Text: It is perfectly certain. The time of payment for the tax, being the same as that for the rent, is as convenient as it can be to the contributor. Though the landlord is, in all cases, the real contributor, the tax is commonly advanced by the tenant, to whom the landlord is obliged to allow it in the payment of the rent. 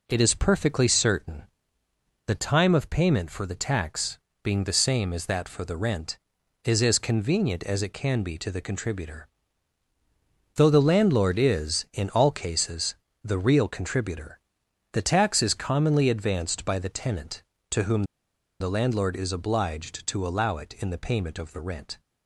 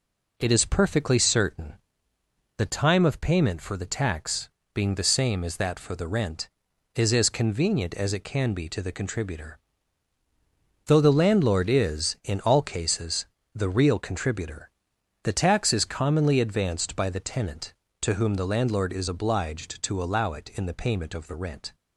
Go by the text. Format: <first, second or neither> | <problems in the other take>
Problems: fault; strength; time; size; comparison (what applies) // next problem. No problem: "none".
second | pauses between "whom" and "the"; noticeable; at 18.0 s; 0.56 s long